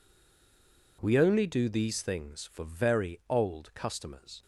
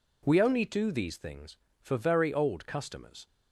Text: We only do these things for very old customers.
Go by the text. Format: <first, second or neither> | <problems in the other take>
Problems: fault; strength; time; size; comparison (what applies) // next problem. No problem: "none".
second | stays silent before the first word; until 0.9 s; 0.9 s long